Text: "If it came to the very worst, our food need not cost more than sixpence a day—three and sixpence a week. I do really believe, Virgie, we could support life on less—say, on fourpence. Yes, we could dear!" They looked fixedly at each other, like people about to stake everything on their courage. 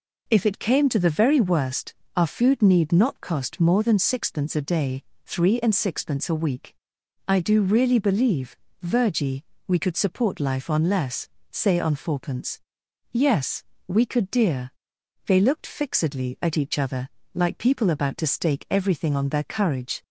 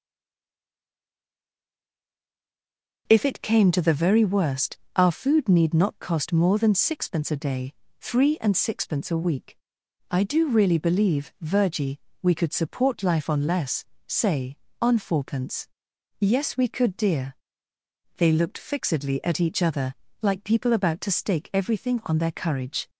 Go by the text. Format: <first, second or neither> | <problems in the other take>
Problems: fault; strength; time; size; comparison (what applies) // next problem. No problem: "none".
first | stays silent before the first word; strong; until 3.0 s; 3.0 s long